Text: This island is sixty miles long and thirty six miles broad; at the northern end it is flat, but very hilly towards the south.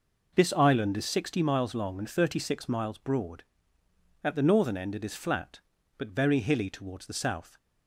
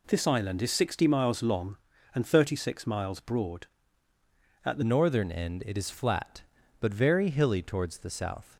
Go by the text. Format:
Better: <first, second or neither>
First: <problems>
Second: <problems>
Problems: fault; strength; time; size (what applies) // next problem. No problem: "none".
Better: first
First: none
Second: changes voice at "northern"; from 4.8 s on; 3.7 s long